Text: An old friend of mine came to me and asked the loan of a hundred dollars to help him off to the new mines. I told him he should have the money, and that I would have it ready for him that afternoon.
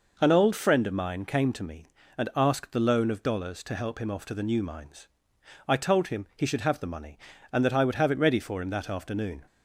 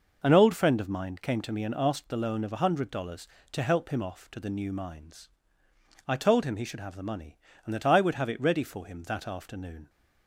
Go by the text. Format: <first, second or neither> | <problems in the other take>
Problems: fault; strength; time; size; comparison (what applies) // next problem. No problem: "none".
second | skips "a hundred"; at 3.2 s